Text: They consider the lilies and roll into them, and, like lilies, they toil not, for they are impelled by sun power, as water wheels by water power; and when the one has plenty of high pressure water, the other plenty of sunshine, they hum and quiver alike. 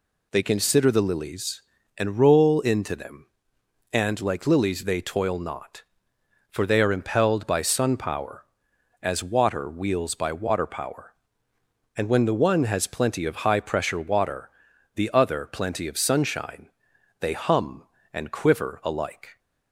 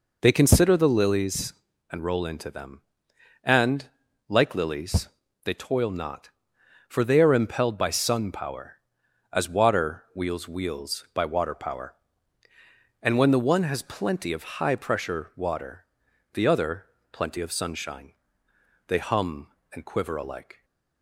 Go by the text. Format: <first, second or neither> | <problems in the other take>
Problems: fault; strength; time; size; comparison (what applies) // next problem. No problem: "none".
first | says "wheels" twice; at 10.4 s // pauses between "other" and "plenty"; slight; at 16.8 s; 0.28 s long